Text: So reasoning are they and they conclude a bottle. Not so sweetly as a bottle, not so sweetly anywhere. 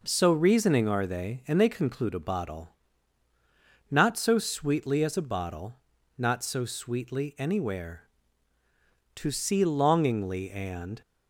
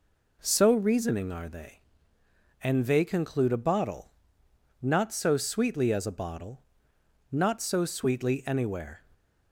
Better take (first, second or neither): second